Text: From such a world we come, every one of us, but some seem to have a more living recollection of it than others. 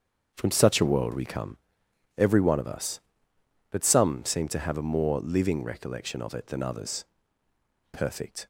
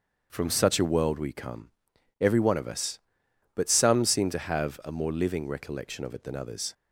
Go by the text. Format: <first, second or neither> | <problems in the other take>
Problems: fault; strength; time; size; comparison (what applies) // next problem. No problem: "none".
second | starts louder than the rest; strong; until 1.3 s; 7 dB; also in the second // goes on to say "Perfect"; from 7.9 s on; 0.54 s long